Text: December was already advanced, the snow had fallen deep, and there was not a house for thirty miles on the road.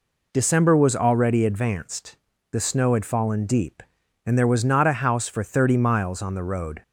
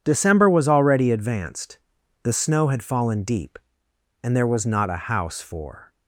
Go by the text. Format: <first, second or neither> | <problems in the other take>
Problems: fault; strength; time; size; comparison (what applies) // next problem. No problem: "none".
first | stops before "thirty miles on the road"; at 5.9 s